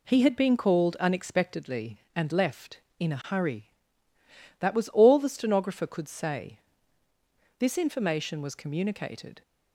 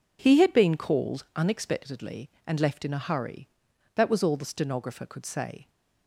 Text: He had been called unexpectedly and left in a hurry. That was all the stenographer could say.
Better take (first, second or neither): second